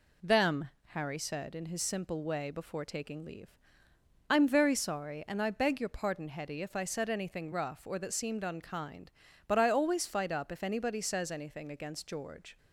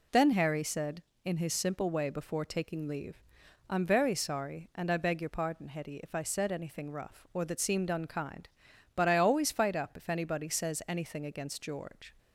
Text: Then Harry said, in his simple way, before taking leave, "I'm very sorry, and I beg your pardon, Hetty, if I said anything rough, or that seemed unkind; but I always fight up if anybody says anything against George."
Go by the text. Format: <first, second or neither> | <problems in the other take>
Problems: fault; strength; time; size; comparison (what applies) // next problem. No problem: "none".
second | says "Them" for "Then"; at 0.2 s